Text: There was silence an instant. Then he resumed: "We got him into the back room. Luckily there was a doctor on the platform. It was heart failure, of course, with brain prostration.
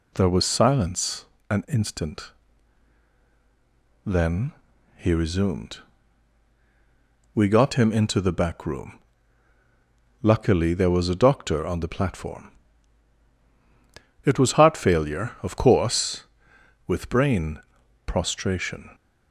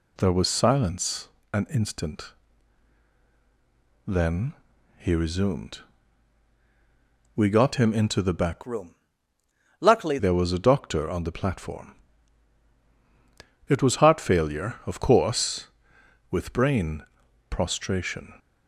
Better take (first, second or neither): first